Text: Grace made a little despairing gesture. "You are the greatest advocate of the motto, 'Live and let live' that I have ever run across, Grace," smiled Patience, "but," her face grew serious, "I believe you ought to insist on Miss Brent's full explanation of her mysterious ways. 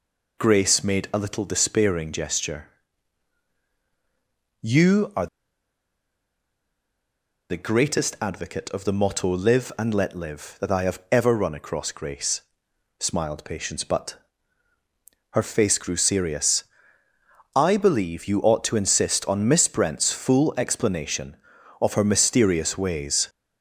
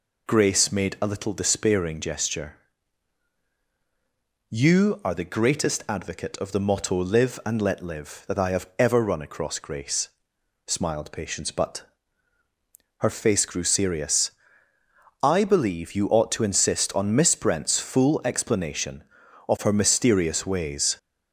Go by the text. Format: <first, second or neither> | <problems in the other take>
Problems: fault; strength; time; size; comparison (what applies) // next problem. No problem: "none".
second | pauses between "are" and "the"; strong; at 5.2 s; 2.2 s long